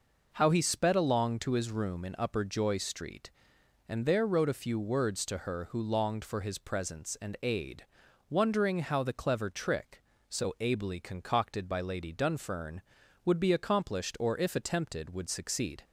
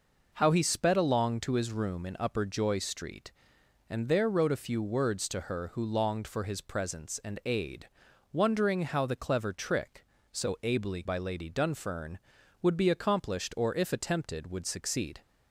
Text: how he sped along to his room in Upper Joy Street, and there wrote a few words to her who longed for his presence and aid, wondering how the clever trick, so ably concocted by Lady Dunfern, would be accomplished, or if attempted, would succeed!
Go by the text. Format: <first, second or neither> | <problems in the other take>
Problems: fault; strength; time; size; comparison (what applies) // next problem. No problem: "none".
first | skips "concocted"; at 11.0 s